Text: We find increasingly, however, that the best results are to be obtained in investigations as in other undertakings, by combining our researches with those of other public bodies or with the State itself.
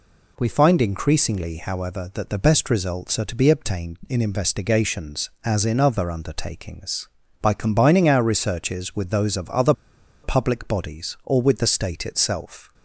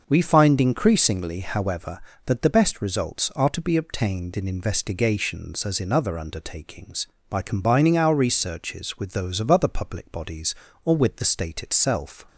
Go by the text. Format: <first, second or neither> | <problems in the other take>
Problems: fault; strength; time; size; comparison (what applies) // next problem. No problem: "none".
second | pauses between "other" and "public"; noticeable; at 9.7 s; 0.50 s long